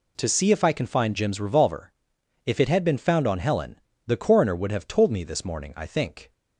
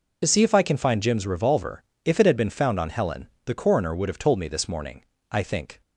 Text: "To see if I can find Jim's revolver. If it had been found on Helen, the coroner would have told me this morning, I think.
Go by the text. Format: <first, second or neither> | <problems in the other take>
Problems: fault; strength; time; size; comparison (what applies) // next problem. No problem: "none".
first | loses the start of "To"; at 0.2 s; 40 ms